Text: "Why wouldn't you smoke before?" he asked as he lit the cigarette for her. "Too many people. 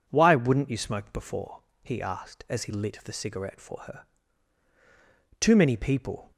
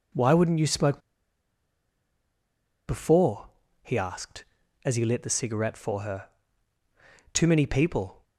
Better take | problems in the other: first | pauses between "smoke" and "before"; strong; at 1.0 s; 1.8 s long

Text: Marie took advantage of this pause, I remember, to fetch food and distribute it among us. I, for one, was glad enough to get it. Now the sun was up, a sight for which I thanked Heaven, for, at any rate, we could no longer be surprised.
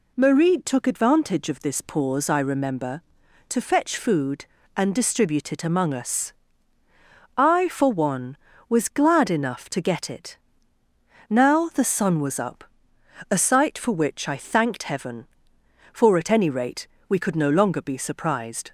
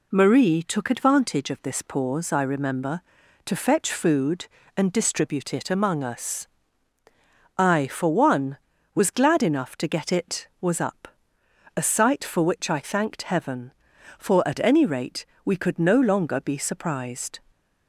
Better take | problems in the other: first | skips "Now the sun"; at 10.5 s

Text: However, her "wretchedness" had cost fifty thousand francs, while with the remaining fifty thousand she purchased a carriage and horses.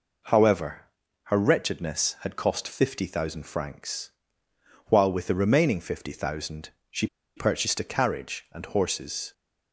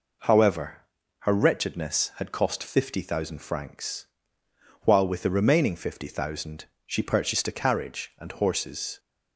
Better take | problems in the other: second | pauses between "thousand" and "she"; slight; at 6.6 s; 0.20 s long; slight in the second // pauses between "she" and "purchased"; slight; at 7.0 s; 0.29 s long

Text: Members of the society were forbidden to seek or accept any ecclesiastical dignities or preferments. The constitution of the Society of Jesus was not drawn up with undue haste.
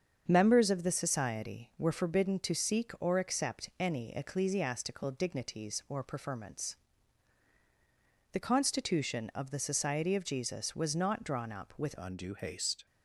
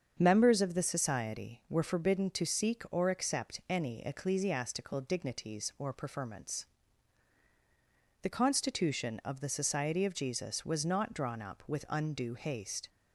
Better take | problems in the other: second | starts louder than the rest; strong; until 1.2 s; 7 dB; strong in the second // changes voice at "undue"; from 11.9 s on; 0.9 s long

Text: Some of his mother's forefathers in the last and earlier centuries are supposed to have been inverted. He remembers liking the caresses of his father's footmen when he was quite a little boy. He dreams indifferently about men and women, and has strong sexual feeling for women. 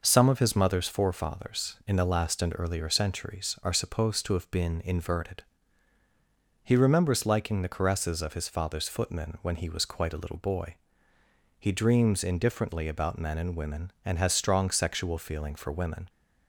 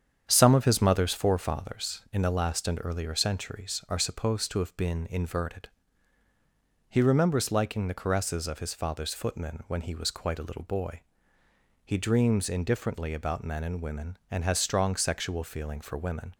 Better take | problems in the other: first | starts louder than the rest; strong; until 1.8 s; 8 dB

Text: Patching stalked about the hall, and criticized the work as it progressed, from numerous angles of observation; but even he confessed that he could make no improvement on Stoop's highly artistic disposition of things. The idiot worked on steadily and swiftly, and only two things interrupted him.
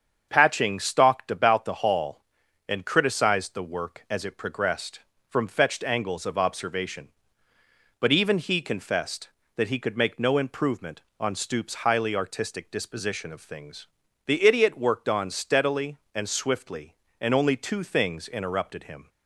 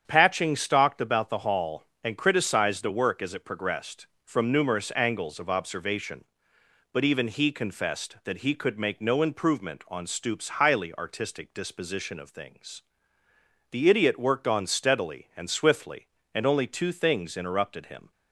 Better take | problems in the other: second | starts louder than the rest; strong; until 1.3 s; 7 dB; strong in the second // says "fetched" for "numerous"; at 5.4 s

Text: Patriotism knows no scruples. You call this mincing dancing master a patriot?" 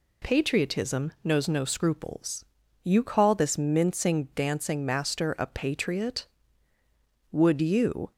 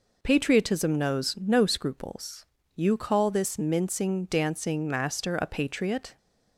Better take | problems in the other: second | goes on to say "Would you"; noticeable; from 7.3 s on; 0.80 s long

